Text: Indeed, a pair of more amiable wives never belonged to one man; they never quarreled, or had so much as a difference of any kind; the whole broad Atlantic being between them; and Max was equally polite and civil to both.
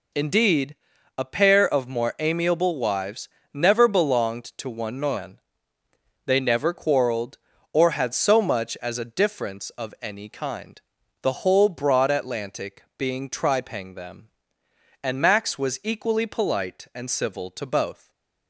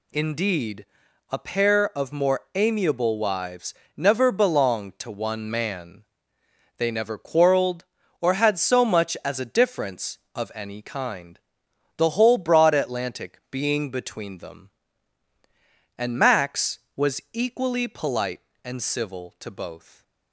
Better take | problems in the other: second | pauses between "wives" and "never"; slight; at 3.2 s; 0.24 s long; slight in the second // pauses between "Atlantic" and "being"; slight; at 12.8 s; 0.16 s long // says "tripang" for "between"; at 13.3 s // stays silent after the last word; slight; from 17.9 s on; 0.5 s long

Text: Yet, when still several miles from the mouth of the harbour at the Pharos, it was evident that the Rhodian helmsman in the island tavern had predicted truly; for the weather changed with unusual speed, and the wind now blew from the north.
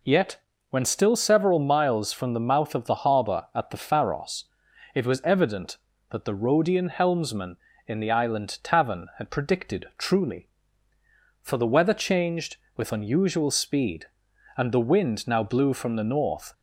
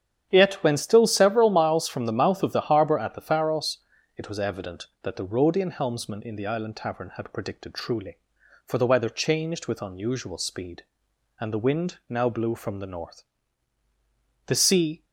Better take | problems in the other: first | starts louder than the rest; strong; until 1.3 s; 9.5 dB // goes on to say "The sea"; from 14.4 s on; 0.58 s long

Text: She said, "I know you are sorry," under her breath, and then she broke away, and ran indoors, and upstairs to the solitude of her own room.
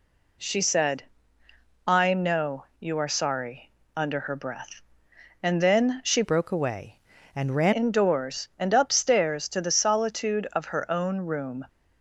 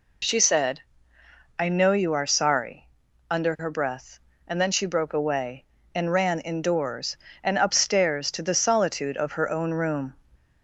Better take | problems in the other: second | changes voice from "broke" to "ran"; from 6.2 to 7.7 s; 1.5 s long

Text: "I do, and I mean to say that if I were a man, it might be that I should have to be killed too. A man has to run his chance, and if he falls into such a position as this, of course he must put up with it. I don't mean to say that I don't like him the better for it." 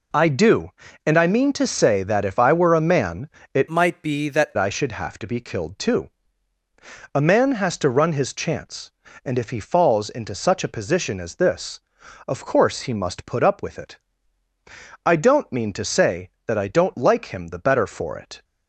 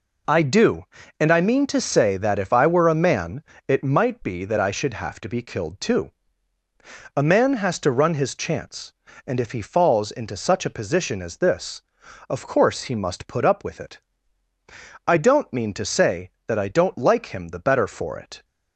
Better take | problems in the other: second | changes voice from "might" to "that"; from 3.6 to 4.5 s; 0.9 s long

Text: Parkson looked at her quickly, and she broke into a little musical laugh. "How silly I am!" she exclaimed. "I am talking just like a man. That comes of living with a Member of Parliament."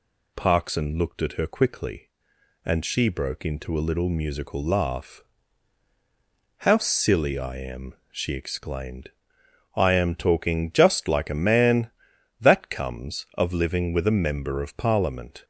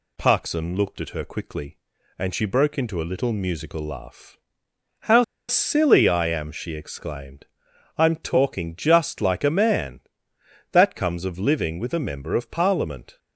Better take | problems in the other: first | pauses between "How" and "silly"; slight; at 5.2 s; 0.24 s long

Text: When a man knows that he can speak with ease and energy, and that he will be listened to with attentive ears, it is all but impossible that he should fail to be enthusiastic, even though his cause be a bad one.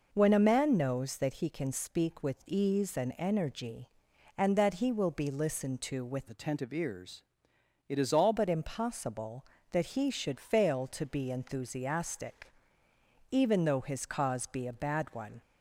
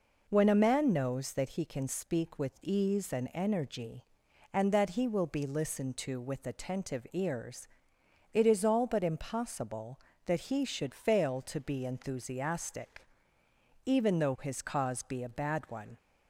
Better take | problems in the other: second | changes voice from "attentive" to "all"; from 6.2 to 8.3 s; 2.1 s long

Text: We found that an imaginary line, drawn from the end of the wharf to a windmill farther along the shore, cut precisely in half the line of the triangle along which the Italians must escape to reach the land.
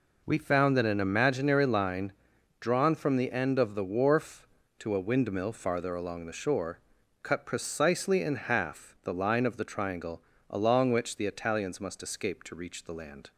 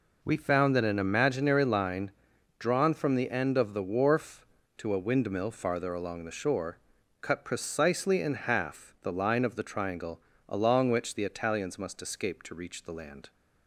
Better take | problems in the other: neither | pauses between "triangle" and "along"; slight; the same in both

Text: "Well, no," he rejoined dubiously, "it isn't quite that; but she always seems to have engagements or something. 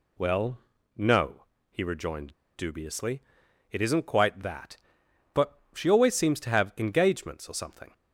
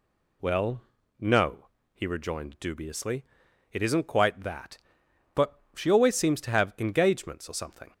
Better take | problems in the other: second | pauses between "rejoined" and "dubiously"; slight; at 2.3 s; 0.22 s long

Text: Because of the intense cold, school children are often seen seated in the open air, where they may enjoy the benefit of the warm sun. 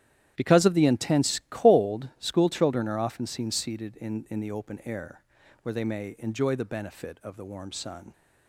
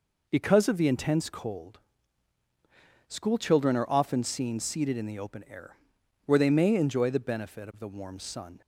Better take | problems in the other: second | starts louder than the rest; strong; until 1.3 s; 11.5 dB // says "in" twice; at 4.2 s

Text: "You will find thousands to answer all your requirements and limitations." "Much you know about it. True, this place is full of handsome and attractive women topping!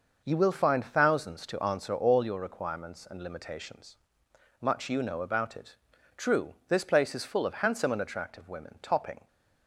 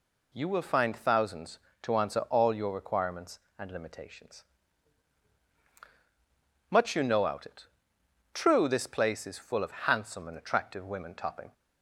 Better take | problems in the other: first | says "out" for "about"; at 7.2 s

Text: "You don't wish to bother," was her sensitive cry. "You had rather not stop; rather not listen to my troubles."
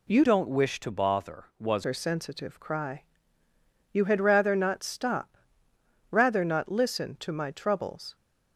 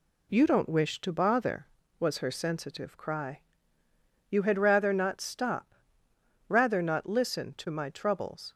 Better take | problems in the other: second | changes voice from "don't" to "was"; from 0.2 to 1.8 s; 1.6 s long

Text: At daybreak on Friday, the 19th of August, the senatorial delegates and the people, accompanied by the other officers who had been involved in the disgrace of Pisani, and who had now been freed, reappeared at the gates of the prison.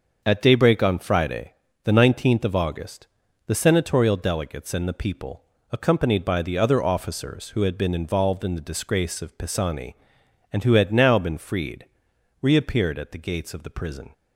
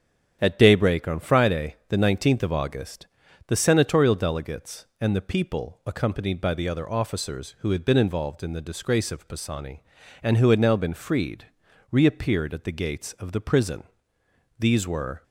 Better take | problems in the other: first | starts louder than the rest; strong; until 1.4 s; 8.5 dB; also in the first // goes on to say "These were"; noticeable; from 14.5 s on; 0.64 s long

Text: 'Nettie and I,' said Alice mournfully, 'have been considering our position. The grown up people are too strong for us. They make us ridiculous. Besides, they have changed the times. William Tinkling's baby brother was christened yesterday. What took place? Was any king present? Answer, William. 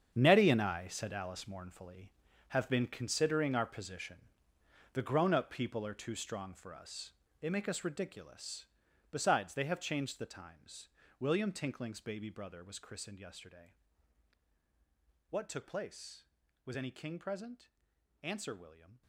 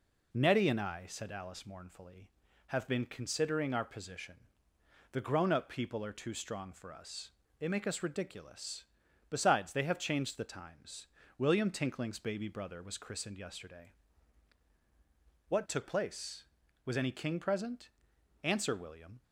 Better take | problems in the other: second | gets quieter; strong; throughout; 12.5 dB

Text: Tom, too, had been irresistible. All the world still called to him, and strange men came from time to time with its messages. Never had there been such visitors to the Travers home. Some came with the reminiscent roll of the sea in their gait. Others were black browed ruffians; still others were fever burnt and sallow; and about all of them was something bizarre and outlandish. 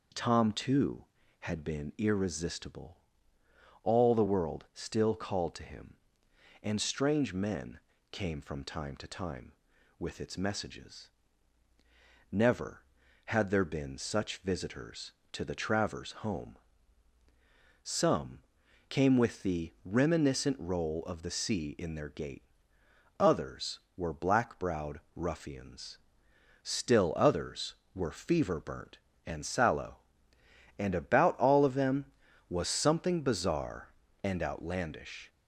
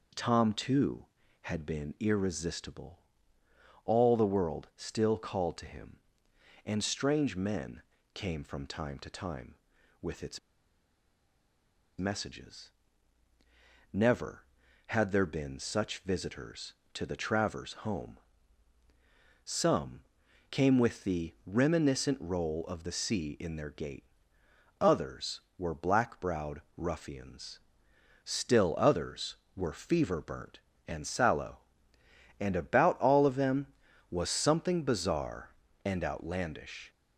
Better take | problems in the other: first | pauses between "men" and "came"; slight; at 7.8 s; 0.32 s long; slight in the first // pauses between "its" and "messages"; strong; at 10.3 s; 1.5 s long // pauses between "Some" and "came"; noticeable; at 20.0 s; 0.50 s long; noticeable in the first // pauses between "browed" and "ruffians"; slight; at 26.6 s; 0.16 s long; slight in the first

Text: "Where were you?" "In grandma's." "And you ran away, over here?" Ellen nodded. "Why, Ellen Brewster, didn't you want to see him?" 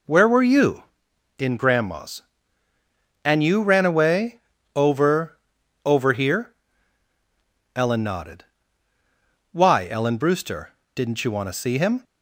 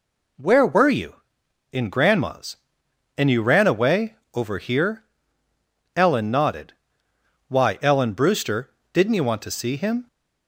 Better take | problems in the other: second | says "over" twice; at 5.8 s

